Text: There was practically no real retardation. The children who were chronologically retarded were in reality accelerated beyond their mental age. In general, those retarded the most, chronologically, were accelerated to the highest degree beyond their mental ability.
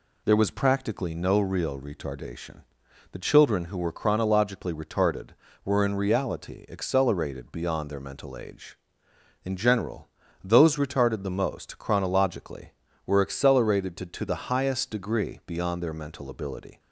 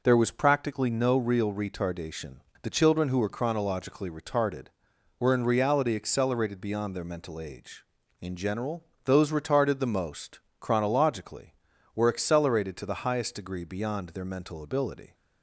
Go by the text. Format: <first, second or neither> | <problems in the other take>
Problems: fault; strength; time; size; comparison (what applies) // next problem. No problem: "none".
second | says "to" twice; at 14.0 s